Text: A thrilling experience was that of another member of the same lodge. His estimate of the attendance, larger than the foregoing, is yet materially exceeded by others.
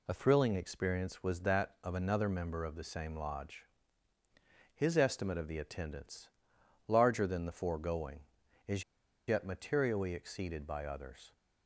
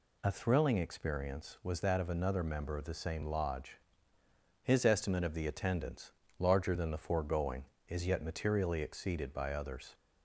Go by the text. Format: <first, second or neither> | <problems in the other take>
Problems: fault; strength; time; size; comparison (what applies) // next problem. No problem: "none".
second | pauses between "is" and "yet"; at 8.8 s; 0.45 s long